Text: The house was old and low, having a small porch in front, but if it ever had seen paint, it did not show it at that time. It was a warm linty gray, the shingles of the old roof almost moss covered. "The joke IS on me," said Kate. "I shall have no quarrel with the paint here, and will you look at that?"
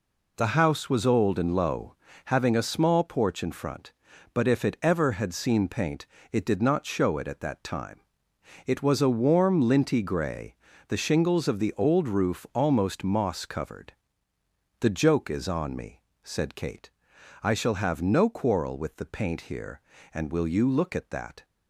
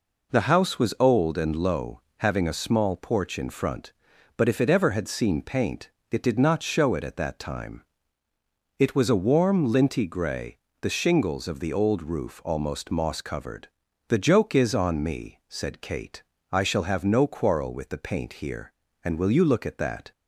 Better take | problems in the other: neither | none

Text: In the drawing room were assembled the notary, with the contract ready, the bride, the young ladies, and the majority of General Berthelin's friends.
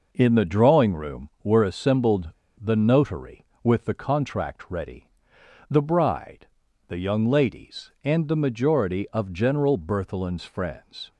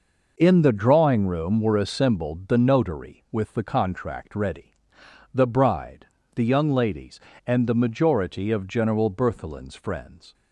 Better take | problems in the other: second | pauses between "assembled" and "the"; slight; at 2.3 s; 0.28 s long

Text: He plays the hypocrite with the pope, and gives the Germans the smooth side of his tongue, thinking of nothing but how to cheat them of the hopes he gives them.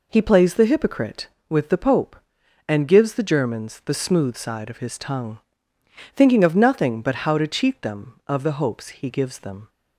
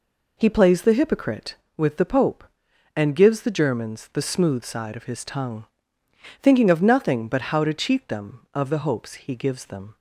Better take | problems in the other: neither | none

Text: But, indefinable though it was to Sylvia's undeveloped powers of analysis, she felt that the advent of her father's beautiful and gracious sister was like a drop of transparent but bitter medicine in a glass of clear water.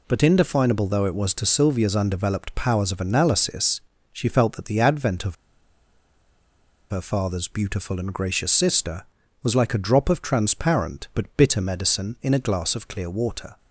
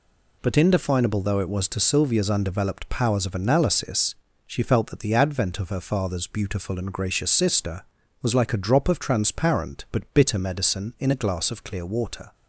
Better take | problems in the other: second | pauses between "of" and "her"; strong; at 5.3 s; 1.5 s long

